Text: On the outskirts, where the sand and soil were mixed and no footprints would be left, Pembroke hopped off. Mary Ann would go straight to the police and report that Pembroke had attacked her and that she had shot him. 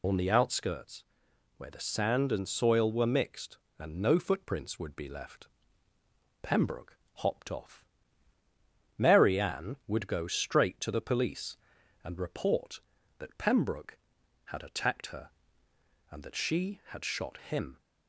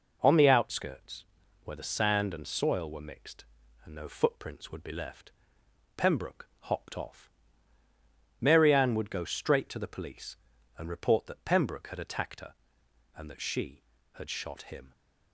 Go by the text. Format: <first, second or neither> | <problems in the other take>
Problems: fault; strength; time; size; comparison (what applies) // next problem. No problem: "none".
second | loses the start of "On"; at 0.0 s; 55 ms // pauses between "Pembroke" and "hopped"; slight; at 6.9 s; 0.20 s long